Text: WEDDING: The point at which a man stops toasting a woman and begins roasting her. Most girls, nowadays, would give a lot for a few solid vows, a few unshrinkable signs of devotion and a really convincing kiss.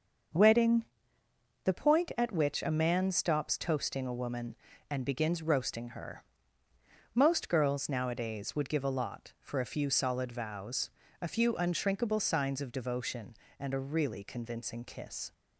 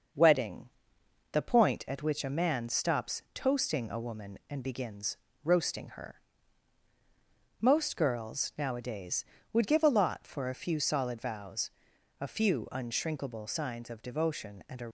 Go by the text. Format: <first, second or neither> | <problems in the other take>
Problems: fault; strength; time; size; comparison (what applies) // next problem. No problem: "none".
first | starts louder than the rest; noticeable; until 1.7 s; 6 dB; also in the first // pauses between "begins" and "roasting"; slight; at 5.1 s; 0.30 s long // stops before "really convincing kiss"; at 14.8 s